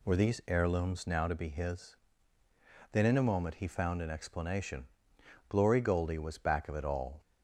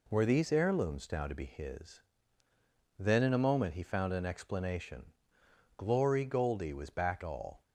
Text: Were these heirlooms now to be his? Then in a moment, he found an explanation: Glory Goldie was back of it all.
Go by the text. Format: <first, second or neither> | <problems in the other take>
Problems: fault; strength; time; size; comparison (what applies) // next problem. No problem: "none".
first | skips "of it"; at 7.2 s